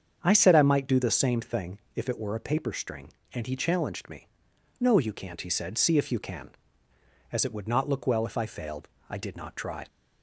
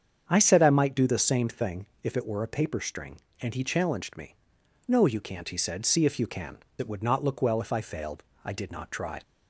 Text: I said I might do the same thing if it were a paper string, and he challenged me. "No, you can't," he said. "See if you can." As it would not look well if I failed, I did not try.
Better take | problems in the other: first | starts louder than the rest; strong; until 1.2 s; 7.5 dB; strong in the first // pauses between "thing" and "if"; slight; at 1.8 s; 0.16 s long; slight in the first // skips "As"; at 6.6 s

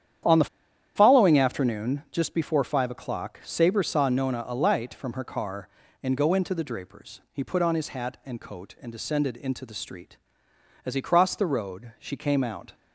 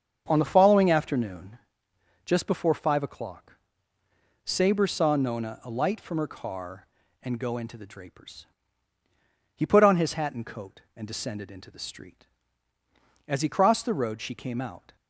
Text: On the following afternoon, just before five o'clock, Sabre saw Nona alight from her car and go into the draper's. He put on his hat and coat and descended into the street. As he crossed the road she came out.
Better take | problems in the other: second | starts louder than the rest; strong; until 1.7 s; 9.5 dB; strong in the second // pauses between "the" and "following"; noticeable; at 0.4 s; 0.49 s long

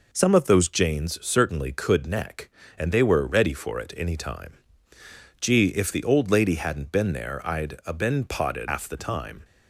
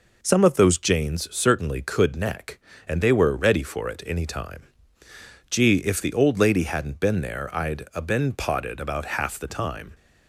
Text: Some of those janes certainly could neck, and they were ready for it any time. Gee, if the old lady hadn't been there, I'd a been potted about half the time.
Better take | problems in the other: second | skips "about"; at 8.6 s

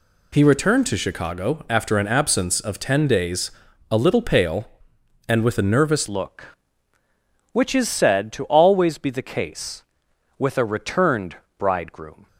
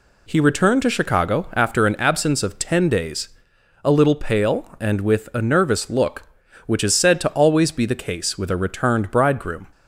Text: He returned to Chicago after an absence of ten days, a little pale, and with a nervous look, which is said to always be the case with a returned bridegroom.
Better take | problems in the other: second | changes voice at "look"; from 6.0 s on; 6.2 s long // pauses between "returned" and "bridegroom"; slight; at 11.3 s; 0.20 s long

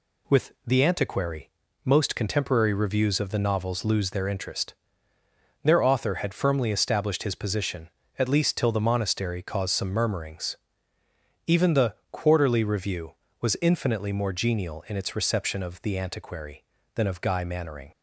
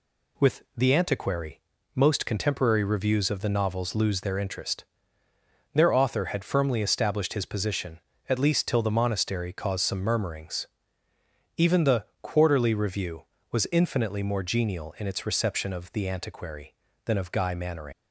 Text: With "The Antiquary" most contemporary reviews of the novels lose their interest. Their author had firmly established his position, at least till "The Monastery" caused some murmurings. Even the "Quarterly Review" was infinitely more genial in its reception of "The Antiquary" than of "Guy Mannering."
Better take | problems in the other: first | pauses between "Antiquary" and "most"; at 1.5 s; 0.38 s long; also in the first // pauses between "the" and "Quarterly"; slight; at 12.0 s; 0.18 s long; slight in the first // leaves "Mannering" unfinished; at 17.9 s; 85 ms

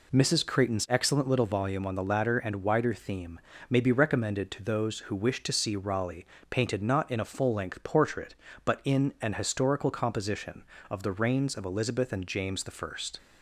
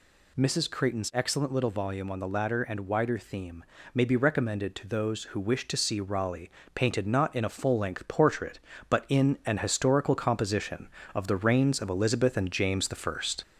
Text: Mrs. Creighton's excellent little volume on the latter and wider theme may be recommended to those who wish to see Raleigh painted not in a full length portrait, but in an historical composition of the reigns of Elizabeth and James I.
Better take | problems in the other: first | gets louder; slight; throughout; 2.5 dB // pauses between "theme" and "may"; slight; at 3.6 s; 0.30 s long; slight in the first // pauses between "Raleigh" and "painted"; slight; at 6.4 s; 0.24 s long; slight in the first

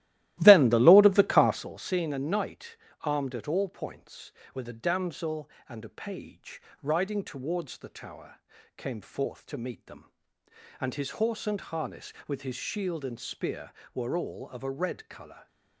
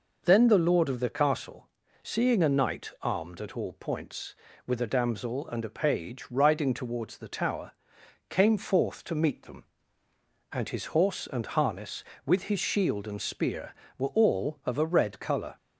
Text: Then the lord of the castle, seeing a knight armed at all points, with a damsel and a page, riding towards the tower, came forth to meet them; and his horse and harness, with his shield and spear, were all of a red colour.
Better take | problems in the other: second | starts louder than the rest; strong; until 1.7 s; 15.5 dB // pauses between "knight" and "armed"; slight; at 2.7 s; 0.24 s long

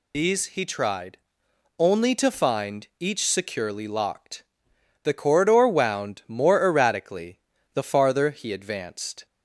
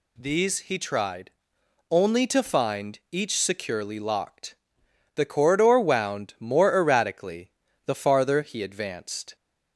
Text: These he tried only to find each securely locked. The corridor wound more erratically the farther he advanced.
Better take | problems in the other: second | loses the start of "These"; at 0.1 s; 115 ms // pauses between "tried" and "only"; noticeable; at 1.1 s; 0.59 s long; noticeable in the second // pauses between "erratically" and "the"; slight; at 7.3 s; 0.34 s long; slight in the second

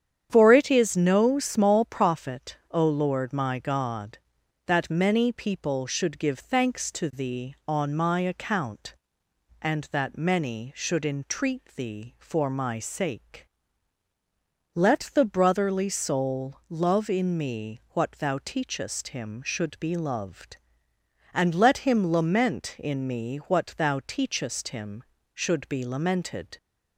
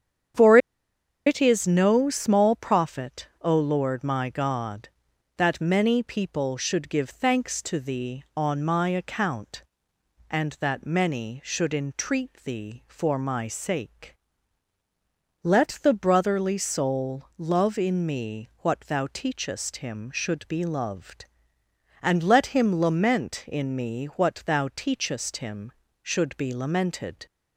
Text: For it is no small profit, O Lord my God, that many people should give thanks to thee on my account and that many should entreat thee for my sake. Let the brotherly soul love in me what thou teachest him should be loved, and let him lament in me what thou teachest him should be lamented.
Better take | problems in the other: first | starts louder than the rest; strong; until 2.0 s; 8.5 dB; strong in the first // pauses between "For" and "it"; noticeable; at 0.5 s; 0.69 s long

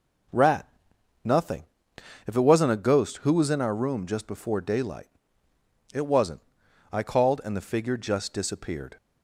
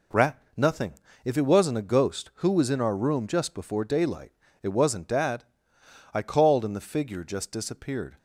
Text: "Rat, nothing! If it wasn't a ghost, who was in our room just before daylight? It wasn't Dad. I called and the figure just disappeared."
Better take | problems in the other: second | skips "Dad"; at 6.6 s

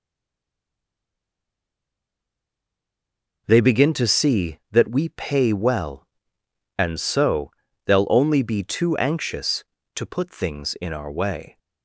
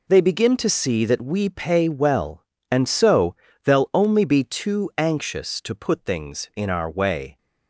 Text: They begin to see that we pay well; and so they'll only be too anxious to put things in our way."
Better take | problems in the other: second | stays silent before the first word; strong; until 3.4 s; 3.4 s long // pauses between "so" and "they'll"; slight; at 7.4 s; 0.34 s long; slight in the second

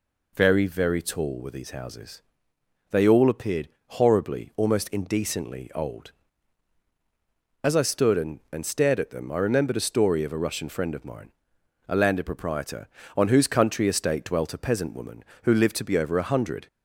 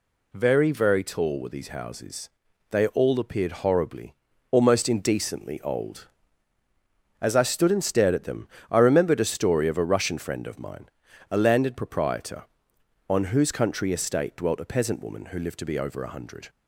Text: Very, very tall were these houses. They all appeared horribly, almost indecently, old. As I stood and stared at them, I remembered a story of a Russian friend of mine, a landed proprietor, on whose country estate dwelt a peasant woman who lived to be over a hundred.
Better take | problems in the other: second | pauses between "appeared" and "horribly"; slight; at 3.6 s; 0.18 s long // says "and" twice; at 8.5 s

